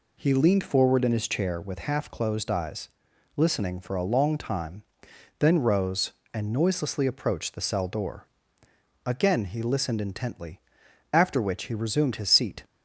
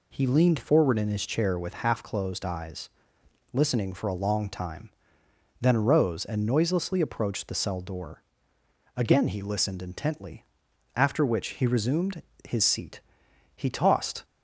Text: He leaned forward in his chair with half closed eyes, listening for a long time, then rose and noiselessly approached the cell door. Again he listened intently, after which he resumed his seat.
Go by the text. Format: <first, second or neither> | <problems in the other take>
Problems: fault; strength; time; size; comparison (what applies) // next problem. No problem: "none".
first | pauses between "resumed" and "his"; slight; at 12.2 s; 0.22 s long // goes on to say "He tossed"; noticeable; from 13.5 s on; 0.68 s long